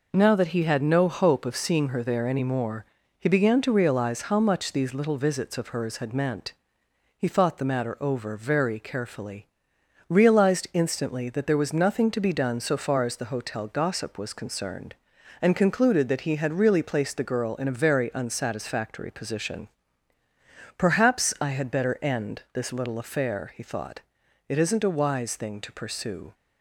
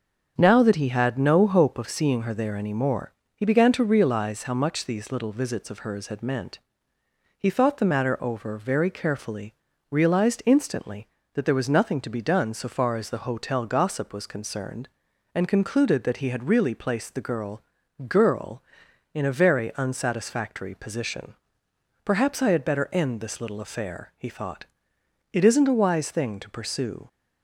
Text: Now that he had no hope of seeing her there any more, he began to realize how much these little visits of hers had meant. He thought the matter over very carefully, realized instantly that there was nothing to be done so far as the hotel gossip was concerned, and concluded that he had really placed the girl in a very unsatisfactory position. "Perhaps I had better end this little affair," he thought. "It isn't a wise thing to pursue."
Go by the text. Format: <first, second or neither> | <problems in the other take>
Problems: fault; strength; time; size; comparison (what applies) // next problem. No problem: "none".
first | starts louder than the rest; until 1.4 s; 7 dB // says "girl" twice; at 18.0 s